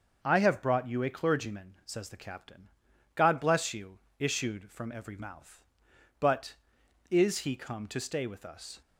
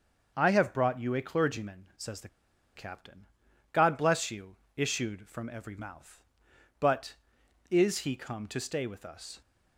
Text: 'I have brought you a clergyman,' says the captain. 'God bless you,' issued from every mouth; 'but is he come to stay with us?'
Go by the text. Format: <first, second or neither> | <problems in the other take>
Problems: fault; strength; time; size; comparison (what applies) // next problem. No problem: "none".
first | starts louder than the rest; until 1.3 s; 6 dB; also in the first // pauses between "the" and "captain"; noticeable; at 2.2 s; 0.48 s long